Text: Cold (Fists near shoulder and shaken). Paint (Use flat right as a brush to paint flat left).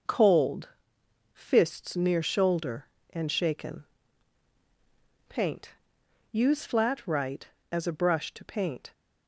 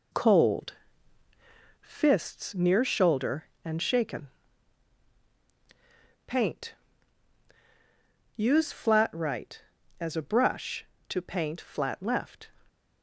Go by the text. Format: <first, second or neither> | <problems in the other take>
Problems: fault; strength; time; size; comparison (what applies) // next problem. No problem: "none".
second | stops before "flat left"; at 8.9 s